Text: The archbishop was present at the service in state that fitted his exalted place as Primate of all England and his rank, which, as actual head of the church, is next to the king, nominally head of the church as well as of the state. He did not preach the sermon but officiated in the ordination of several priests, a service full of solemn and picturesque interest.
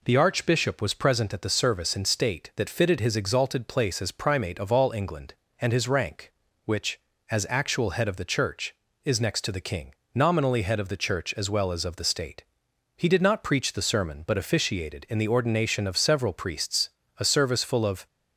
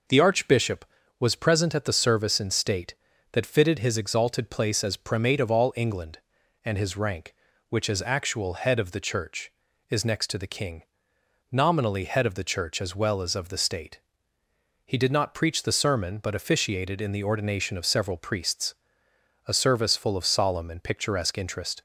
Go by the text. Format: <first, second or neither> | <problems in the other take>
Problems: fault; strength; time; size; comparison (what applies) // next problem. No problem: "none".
second | stops before "solemn and picturesque interest"; at 18.0 s